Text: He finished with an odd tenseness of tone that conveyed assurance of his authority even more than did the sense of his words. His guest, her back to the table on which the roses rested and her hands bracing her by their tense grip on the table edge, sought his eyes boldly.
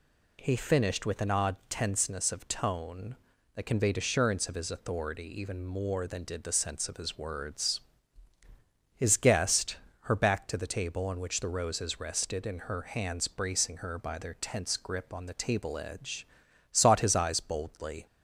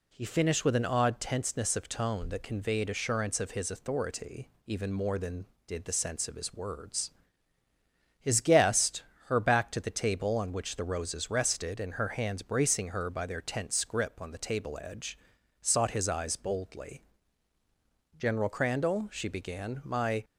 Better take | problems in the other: first | pauses between "authority" and "even"; slight; at 4.5 s; 0.16 s long // goes on to say "General Crandall she began my"; strong; from 18.1 s on; 2.0 s long

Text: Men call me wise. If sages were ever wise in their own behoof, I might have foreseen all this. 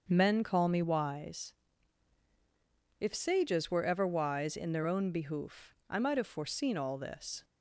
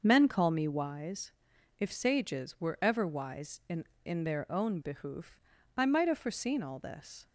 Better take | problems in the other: first | starts louder than the rest; noticeable; until 1.0 s; 6 dB; also in the first // says "in" twice; at 4.0 s

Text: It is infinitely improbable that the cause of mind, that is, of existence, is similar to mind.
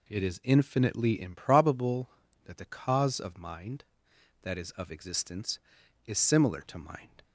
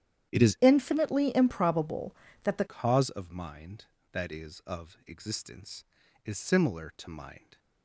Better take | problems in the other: first | starts louder than the rest; strong; until 1.3 s; 10.5 dB // changes voice from "infinitely" to "the"; from 0.6 to 2.6 s; 2.0 s long

